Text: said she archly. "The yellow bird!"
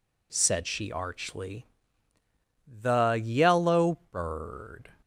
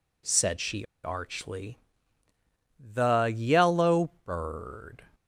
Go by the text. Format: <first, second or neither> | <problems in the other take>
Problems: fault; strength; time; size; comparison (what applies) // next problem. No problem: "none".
first | pauses between "she" and "archly"; slight; at 0.8 s; 0.18 s long